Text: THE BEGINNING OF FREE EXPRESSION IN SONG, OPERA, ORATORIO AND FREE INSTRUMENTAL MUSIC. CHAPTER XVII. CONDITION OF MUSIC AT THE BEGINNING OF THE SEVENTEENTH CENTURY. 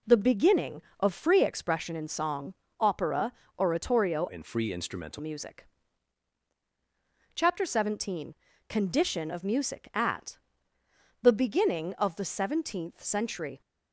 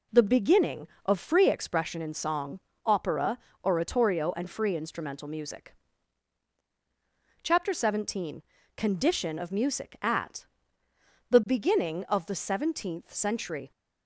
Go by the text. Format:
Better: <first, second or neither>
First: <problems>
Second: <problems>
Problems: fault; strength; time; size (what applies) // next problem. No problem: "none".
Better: second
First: changes voice from "AND" to "INSTRUMENTAL"; from 4.2 to 5.1 s; 0.9 s long // pauses between "AT" and "THE"; noticeable; at 10.3 s; 0.82 s long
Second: pauses between "AT" and "THE"; noticeable; at 10.4 s; 0.82 s long